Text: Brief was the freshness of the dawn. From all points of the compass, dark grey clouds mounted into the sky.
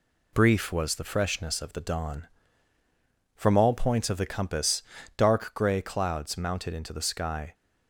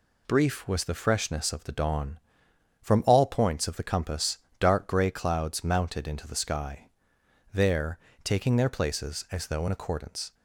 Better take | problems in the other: first | goes on to say "There taking their places as though in accordance"; strong; from 7.5 s on; 2.8 s long

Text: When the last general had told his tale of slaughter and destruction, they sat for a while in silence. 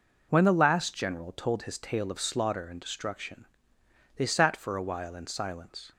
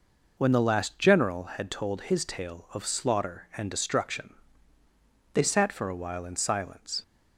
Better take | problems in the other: second | skips "had"; at 1.3 s

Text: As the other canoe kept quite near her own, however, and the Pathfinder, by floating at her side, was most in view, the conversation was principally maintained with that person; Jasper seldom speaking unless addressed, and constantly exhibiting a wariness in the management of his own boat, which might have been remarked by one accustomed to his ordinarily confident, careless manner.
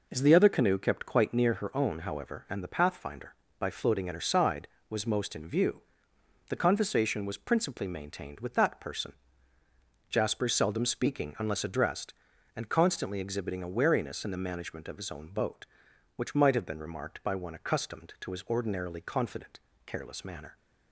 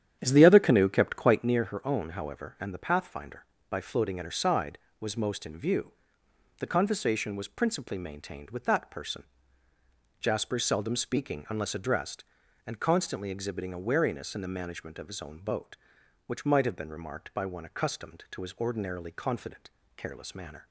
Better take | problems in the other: first | starts louder than the rest; strong; until 1.6 s; 9.5 dB

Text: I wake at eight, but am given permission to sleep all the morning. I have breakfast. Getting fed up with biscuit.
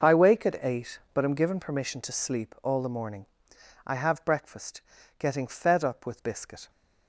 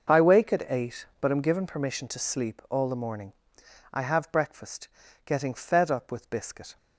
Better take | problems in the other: neither | none

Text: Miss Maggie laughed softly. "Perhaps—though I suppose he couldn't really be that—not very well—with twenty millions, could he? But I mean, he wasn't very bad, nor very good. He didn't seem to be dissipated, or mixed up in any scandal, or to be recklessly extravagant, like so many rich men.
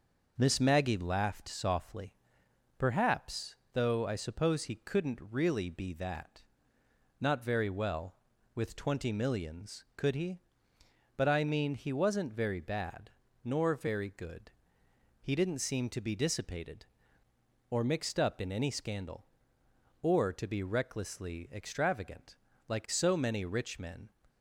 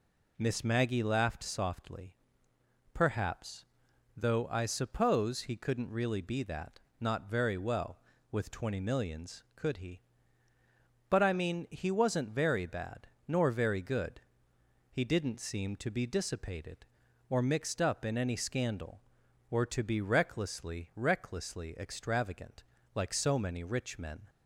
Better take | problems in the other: first | says "recklessly" twice; at 20.9 s

